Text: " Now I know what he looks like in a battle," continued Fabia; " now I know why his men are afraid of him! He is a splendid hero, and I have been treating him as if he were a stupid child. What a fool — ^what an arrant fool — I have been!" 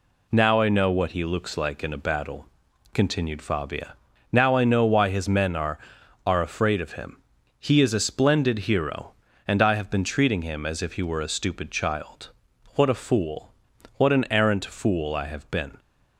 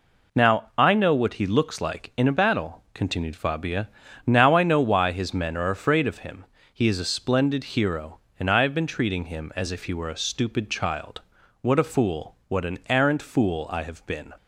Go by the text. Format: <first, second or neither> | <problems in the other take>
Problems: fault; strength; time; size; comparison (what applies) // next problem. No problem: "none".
second | says "are" twice; at 6.2 s